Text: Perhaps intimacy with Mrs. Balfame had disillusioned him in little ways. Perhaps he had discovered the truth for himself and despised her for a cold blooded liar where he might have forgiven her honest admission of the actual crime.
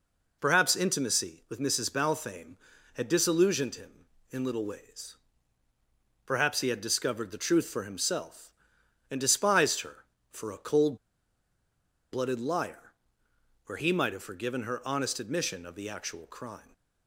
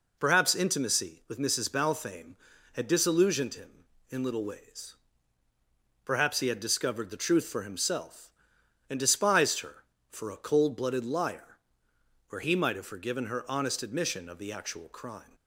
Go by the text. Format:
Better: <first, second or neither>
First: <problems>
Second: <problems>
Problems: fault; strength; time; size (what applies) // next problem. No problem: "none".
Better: second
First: pauses between "cold" and "blooded"; at 10.9 s; 1.1 s long // pauses between "liar" and "where"; noticeable; at 12.9 s; 0.74 s long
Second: pauses between "liar" and "where"; noticeable; at 11.5 s; 0.72 s long